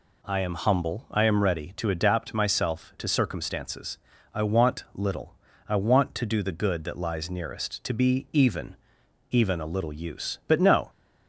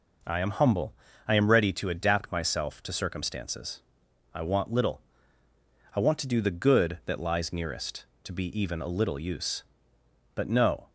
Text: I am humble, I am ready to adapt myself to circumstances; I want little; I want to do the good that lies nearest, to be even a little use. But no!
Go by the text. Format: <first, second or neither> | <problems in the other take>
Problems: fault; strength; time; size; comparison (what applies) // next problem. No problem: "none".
second | says "even" twice; at 9.3 s